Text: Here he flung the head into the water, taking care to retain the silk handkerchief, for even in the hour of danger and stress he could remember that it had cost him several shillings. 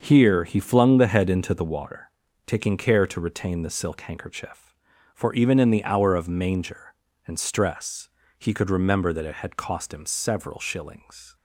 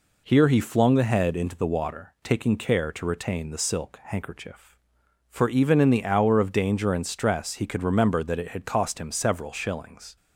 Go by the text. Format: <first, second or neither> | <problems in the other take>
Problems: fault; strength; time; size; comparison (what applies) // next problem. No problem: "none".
second | starts louder than the rest; until 1.0 s; 7 dB // says "manger" for "danger"; at 6.2 s // pauses between "stress" and "he"; slight; at 8.0 s; 0.30 s long